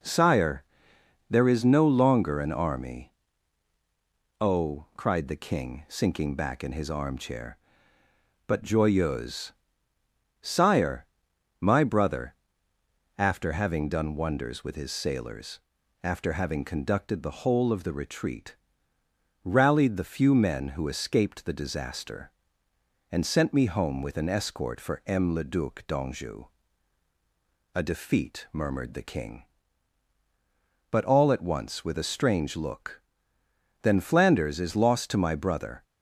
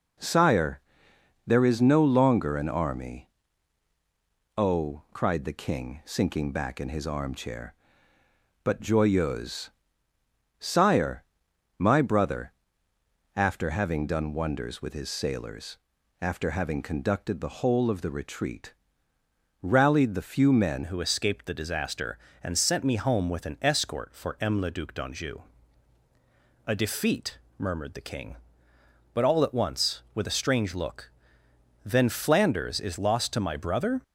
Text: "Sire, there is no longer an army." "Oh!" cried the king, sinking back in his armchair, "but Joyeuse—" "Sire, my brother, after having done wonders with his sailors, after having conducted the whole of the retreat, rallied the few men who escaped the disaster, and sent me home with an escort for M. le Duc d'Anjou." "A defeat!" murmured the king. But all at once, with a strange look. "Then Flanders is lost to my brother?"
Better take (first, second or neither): first